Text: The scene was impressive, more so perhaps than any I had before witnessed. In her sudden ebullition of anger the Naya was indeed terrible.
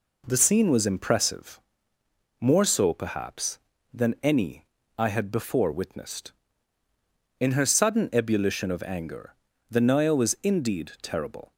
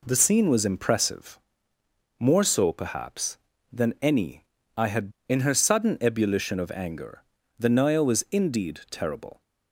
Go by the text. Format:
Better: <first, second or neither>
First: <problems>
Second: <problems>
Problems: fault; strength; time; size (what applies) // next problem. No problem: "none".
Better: first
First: pauses between "any" and "I"; slight; at 4.6 s; 0.32 s long // pauses between "anger" and "the"; slight; at 9.3 s; 0.36 s long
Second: pauses between "any" and "I"; slight; at 4.4 s; 0.32 s long // skips "before witnessed"; at 5.1 s // pauses between "anger" and "the"; slight; at 7.2 s; 0.36 s long